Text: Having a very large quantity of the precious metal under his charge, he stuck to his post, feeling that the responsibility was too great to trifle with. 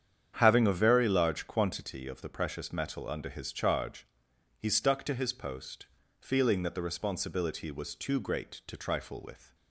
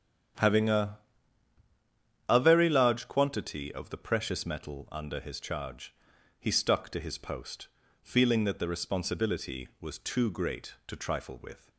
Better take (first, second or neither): first